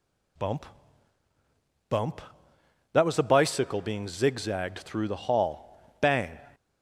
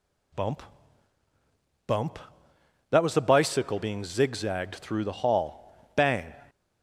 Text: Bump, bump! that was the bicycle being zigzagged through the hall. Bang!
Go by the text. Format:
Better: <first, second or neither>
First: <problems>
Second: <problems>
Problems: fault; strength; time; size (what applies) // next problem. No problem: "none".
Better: neither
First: none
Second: none